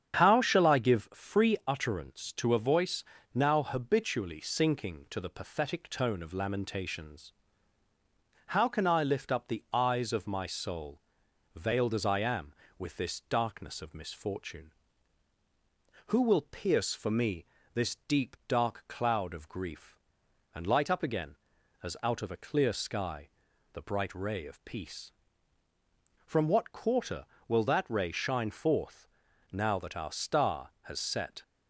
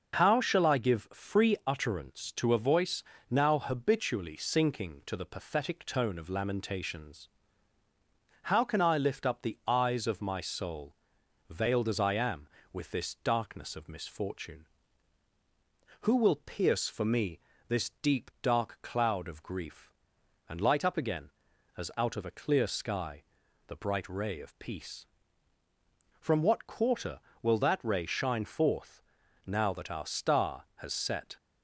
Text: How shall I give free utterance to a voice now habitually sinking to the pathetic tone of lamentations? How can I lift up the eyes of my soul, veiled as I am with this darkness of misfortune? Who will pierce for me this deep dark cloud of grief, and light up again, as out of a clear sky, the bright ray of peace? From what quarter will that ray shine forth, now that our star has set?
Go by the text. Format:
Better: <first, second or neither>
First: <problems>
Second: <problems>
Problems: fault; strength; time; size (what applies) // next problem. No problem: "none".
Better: second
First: starts louder than the rest; strong; until 1.1 s; 8 dB // pauses between "voice" and "now"; slight; at 3.0 s; 0.31 s long // pauses between "me" and "this"; slight; at 17.4 s; 0.30 s long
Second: pauses between "voice" and "now"; slight; at 3.0 s; 0.28 s long // pauses between "me" and "this"; slight; at 17.3 s; 0.30 s long